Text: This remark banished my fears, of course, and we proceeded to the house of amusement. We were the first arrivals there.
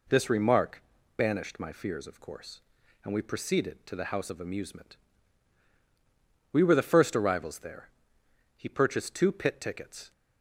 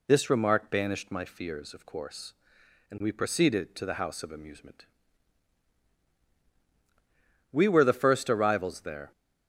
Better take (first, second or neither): second